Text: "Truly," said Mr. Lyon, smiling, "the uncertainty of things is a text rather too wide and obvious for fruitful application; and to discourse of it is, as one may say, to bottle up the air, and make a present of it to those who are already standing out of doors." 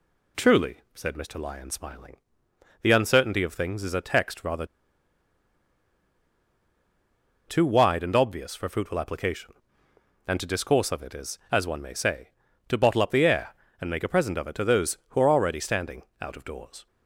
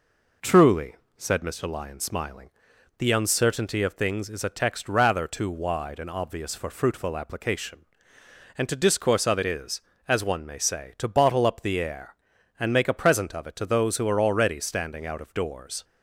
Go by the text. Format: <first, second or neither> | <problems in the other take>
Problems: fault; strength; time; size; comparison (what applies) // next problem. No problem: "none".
second | pauses between "rather" and "too"; strong; at 4.6 s; 2.8 s long // pauses between "standing" and "out"; slight; at 16.0 s; 0.18 s long